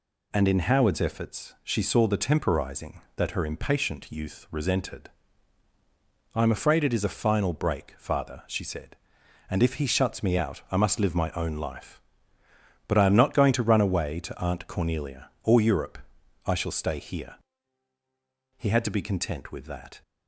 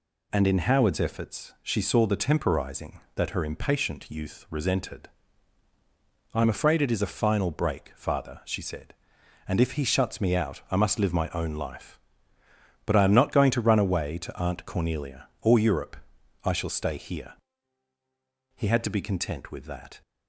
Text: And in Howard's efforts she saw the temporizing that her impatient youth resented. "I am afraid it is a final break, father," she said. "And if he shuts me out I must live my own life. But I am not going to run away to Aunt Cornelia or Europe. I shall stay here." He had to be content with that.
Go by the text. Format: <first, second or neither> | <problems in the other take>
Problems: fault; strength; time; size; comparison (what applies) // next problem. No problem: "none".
neither | none